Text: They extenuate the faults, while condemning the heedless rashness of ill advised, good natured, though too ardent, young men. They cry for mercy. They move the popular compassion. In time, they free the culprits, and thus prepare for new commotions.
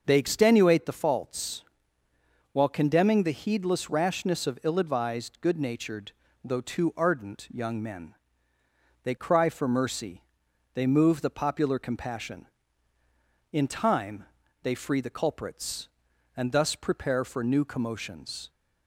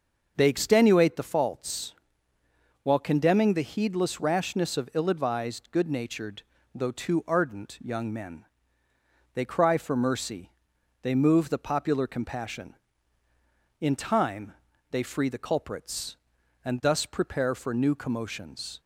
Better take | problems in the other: neither | starts louder than the rest; the same in both

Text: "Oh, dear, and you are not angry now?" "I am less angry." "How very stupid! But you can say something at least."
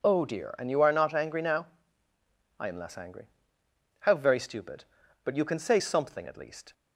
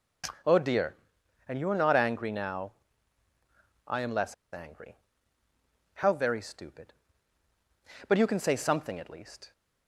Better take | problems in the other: first | starts louder than the rest; noticeable; until 1.9 s; 6 dB // pauses between "less" and "angry"; slight; at 4.3 s; 0.17 s long

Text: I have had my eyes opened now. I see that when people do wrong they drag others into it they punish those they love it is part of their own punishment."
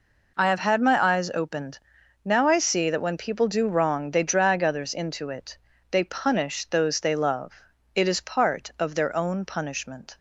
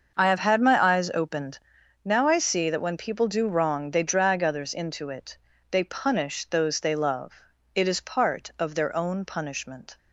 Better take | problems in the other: first | starts louder than the rest; until 1.7 s; 6.5 dB // pauses between "opened" and "now"; noticeable; at 1.5 s; 0.48 s long; noticeable in the first // pauses between "it" and "they"; slight; at 5.3 s; 0.36 s long; slight in the first // pauses between "love" and "it"; at 7.3 s; 0.40 s long; also in the first

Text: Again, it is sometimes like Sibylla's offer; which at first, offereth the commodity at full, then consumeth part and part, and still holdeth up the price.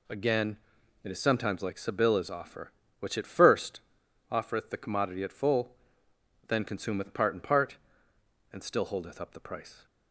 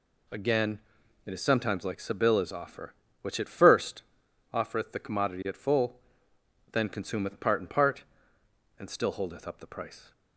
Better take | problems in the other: neither | none

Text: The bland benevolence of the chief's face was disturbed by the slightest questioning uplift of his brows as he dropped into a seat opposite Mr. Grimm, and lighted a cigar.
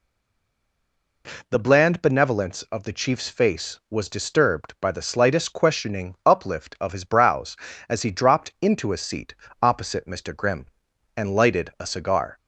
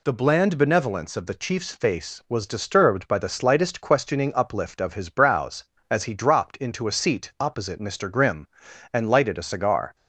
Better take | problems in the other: second | stays silent before the first word; noticeable; until 1.2 s; 1.2 s long // pauses between "seat" and "opposite"; slight; at 9.3 s; 0.26 s long

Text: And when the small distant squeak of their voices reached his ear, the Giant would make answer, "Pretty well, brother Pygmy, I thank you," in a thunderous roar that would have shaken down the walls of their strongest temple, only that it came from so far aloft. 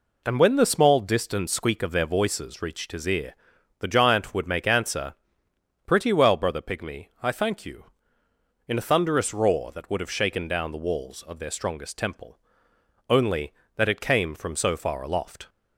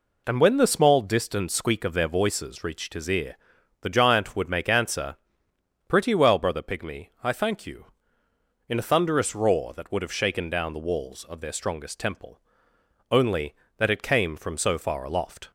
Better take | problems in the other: neither | none

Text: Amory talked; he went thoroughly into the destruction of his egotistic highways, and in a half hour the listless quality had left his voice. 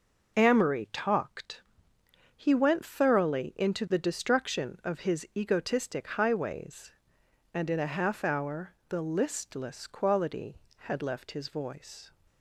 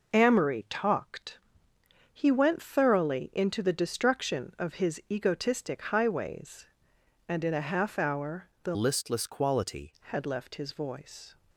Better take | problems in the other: first | pauses between "hour" and "the"; slight; at 8.4 s; 0.16 s long; slight in the first // changes voice from "listless" to "quality"; from 8.7 to 9.9 s; 1.2 s long

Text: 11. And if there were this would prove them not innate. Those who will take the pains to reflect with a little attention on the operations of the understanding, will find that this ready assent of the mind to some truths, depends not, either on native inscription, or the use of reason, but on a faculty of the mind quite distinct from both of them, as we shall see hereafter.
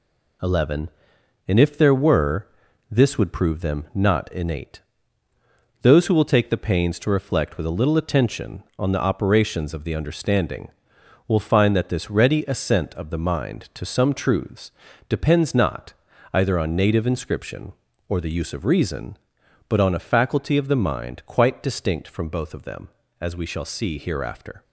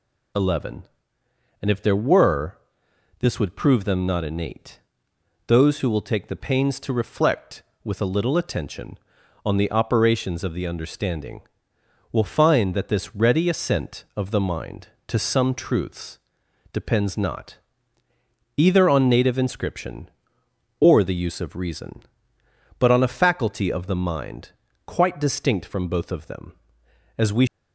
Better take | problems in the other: first | pauses between "were" and "this"; noticeable; at 2.5 s; 0.62 s long; noticeable in the first // pauses between "mind" and "quite"; slight; at 24.5 s; 0.36 s long // stops before "shall see hereafter"; at 27.4 s

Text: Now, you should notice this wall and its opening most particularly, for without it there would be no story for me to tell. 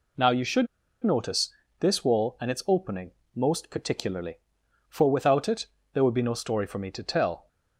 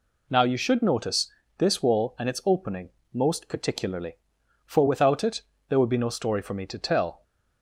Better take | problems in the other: second | pauses between "should" and "notice"; at 0.6 s; 0.36 s long // pauses between "notice" and "this"; slight; at 1.4 s; 0.30 s long; slight in the second // pauses between "opening" and "most"; slight; at 3.1 s; 0.24 s long; slight in the second // pauses between "it" and "there"; slight; at 5.6 s; 0.26 s long; slight in the second

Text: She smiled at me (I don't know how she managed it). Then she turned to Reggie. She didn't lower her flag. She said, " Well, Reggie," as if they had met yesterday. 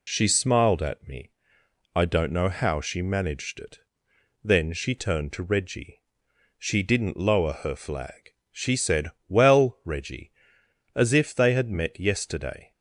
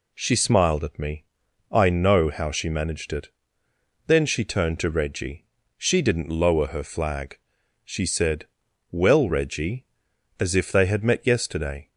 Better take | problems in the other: first | skips "don't"; at 1.8 s

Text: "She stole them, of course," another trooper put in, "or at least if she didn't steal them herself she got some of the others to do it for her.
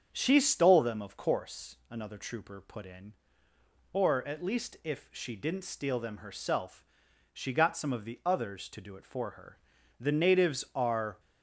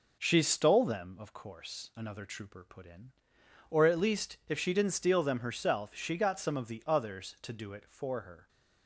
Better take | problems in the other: second | starts louder than the rest; strong; until 1.1 s; 7 dB // pauses between "herself" and "she"; noticeable; at 6.8 s; 0.48 s long // goes on to say "The natives are"; noticeable; from 9.9 s on; 1.2 s long

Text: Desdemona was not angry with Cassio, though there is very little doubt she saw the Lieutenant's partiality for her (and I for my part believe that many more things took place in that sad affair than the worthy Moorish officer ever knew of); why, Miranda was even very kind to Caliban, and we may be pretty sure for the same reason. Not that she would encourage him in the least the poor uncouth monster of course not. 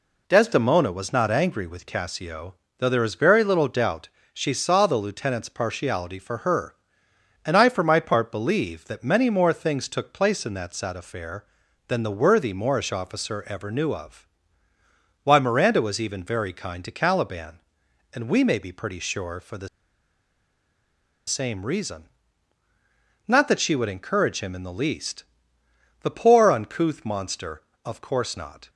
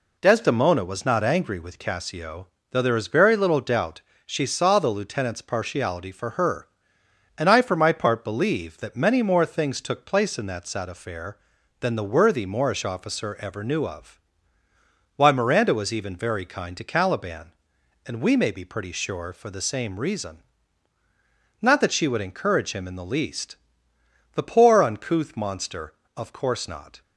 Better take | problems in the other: second | pauses between "doubt" and "she"; slight; at 4.0 s; 0.24 s long; slight in the second // pauses between "the" and "same"; strong; at 19.6 s; 1.5 s long // pauses between "least" and "the"; noticeable; at 25.2 s; 0.74 s long; noticeable in the second

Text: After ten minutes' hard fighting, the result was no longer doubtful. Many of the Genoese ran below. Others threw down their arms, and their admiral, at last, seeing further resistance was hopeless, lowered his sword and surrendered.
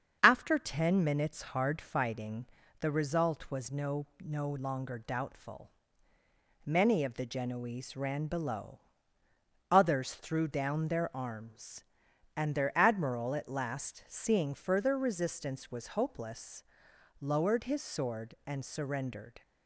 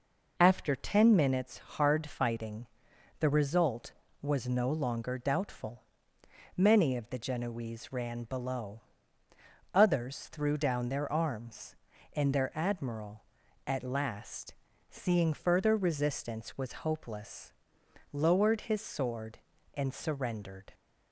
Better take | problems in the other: second | starts louder than the rest; strong; until 1.2 s; 7.5 dB // says "no" twice; at 4.1 s

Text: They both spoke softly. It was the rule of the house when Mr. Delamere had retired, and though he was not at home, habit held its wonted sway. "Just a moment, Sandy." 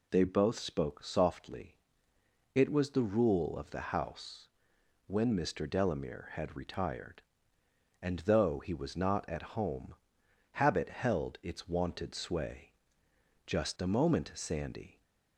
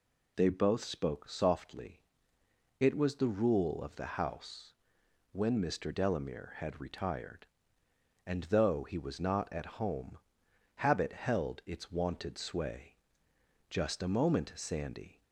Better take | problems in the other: neither | pauses between "house" and "when"; noticeable; the same in both

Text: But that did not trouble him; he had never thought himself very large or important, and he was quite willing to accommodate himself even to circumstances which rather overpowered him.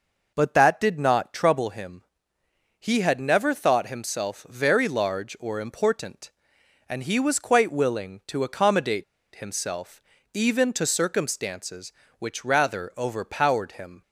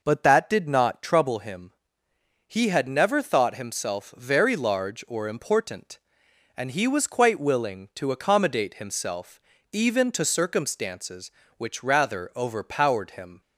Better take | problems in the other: second | pauses between "accommodate" and "himself"; slight; at 9.0 s; 0.31 s long // pauses between "himself" and "even"; slight; at 10.0 s; 0.32 s long; slight in the second

